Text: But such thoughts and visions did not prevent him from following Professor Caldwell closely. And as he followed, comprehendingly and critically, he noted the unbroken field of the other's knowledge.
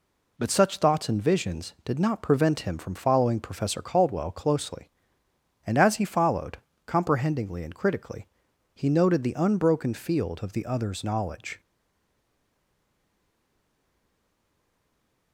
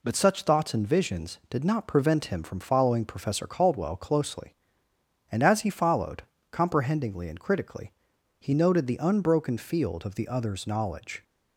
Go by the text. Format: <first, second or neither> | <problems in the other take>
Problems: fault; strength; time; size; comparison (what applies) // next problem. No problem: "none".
second | stays silent after the last word; strong; from 11.5 s on; 3.8 s long